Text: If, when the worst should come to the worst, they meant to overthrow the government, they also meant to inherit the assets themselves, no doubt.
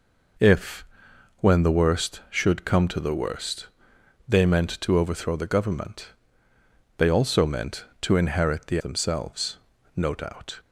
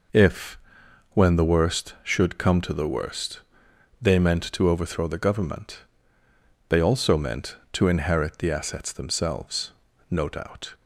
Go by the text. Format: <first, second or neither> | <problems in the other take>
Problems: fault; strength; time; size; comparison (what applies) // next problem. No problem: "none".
second | skips "assets"; at 8.7 s